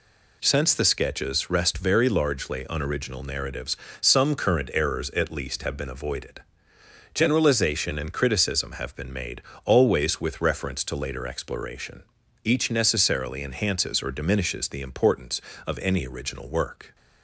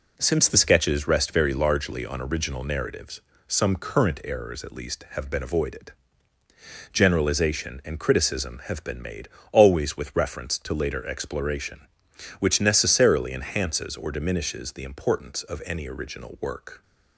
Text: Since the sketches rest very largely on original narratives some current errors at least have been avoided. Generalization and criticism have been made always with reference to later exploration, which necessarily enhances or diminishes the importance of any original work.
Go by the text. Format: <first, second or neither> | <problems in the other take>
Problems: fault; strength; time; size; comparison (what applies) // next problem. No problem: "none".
second | pauses between "narratives" and "some"; slight; at 3.7 s; 0.24 s long; slight in the second // pauses between "made" and "always"; slight; at 9.4 s; 0.22 s long; slight in the second // says "each" for "which"; at 12.4 s